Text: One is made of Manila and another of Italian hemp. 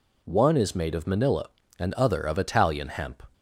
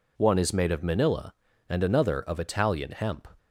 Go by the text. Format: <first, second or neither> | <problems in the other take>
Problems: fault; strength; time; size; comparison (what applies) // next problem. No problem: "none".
second | says "other" for "another"; at 1.9 s